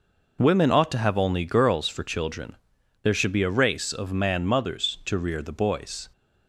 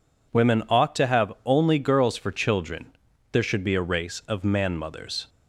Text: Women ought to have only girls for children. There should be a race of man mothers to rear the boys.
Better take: first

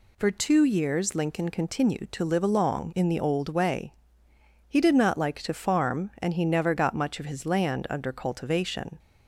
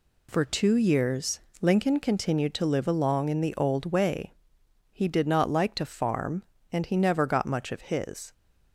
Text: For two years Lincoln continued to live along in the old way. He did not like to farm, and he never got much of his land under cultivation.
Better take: first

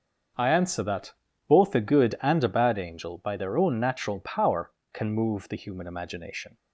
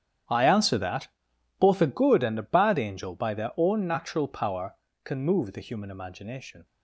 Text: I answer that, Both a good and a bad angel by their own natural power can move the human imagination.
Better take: first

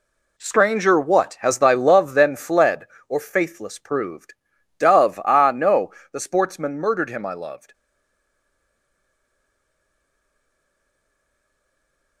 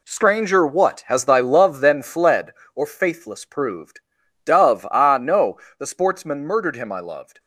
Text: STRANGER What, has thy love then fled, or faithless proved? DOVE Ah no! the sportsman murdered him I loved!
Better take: second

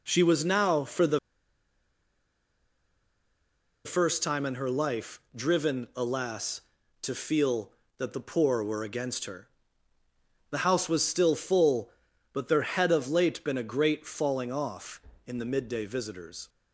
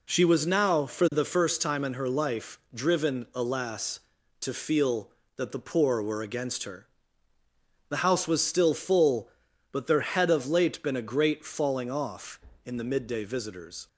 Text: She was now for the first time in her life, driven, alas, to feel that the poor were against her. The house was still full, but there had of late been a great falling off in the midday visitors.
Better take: second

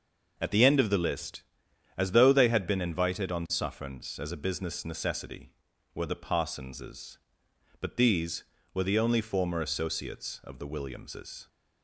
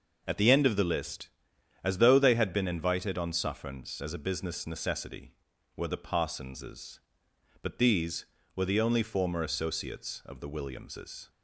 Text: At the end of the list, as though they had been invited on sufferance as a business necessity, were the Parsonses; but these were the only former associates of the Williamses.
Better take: neither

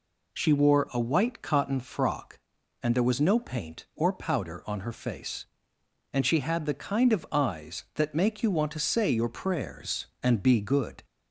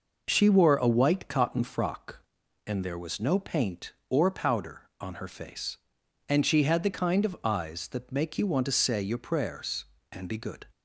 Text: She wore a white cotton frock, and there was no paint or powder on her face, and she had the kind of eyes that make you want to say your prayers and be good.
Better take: neither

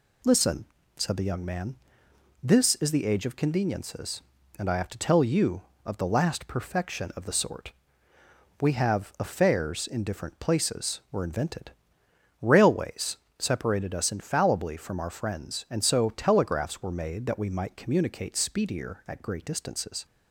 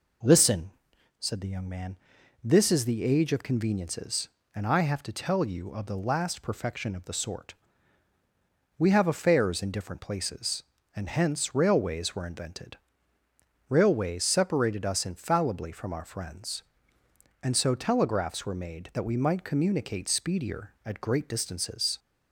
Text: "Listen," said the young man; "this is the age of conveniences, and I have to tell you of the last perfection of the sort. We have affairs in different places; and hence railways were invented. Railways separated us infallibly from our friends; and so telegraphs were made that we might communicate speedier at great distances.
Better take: second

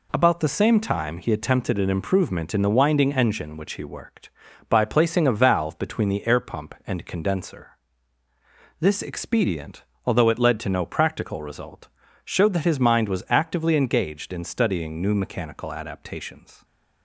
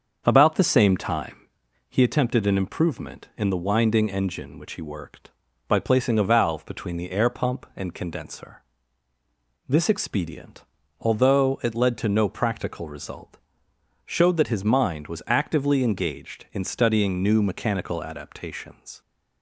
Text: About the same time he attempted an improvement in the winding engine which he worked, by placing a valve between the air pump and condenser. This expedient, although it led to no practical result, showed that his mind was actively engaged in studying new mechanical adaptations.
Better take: first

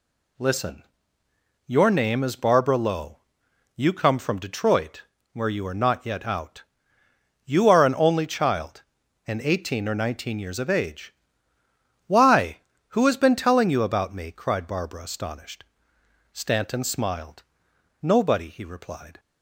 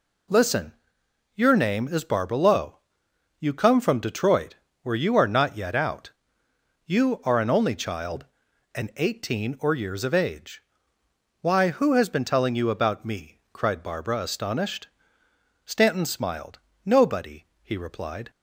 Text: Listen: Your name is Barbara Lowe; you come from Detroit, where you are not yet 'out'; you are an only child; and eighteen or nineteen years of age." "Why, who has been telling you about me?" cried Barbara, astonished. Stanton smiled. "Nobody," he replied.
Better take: first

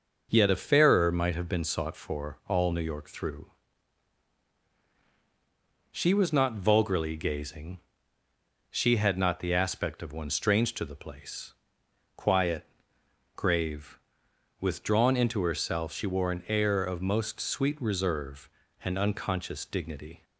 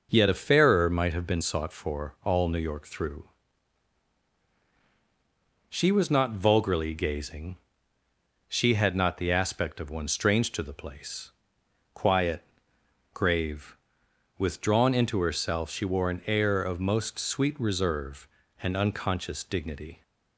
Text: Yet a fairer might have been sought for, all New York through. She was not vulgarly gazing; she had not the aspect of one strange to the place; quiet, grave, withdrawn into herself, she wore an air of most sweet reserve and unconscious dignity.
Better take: neither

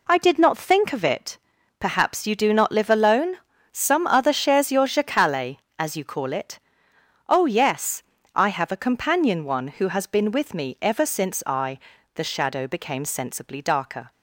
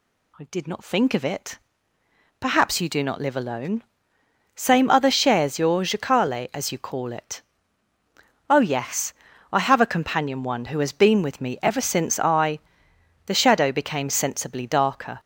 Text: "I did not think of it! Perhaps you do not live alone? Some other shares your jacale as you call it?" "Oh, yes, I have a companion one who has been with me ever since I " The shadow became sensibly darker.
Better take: first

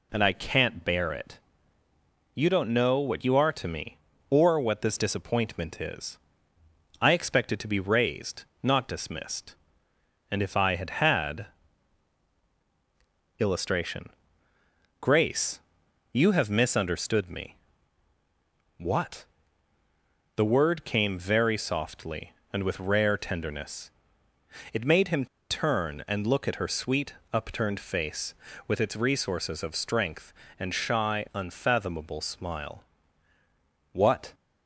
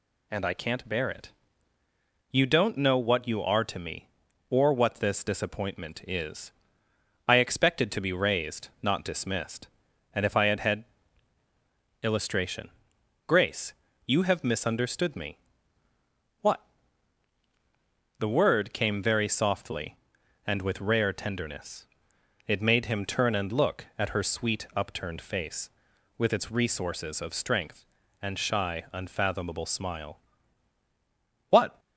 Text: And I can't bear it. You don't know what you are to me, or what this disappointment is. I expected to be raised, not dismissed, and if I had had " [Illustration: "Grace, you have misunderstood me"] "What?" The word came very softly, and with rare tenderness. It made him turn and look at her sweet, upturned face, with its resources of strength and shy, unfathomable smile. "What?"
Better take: second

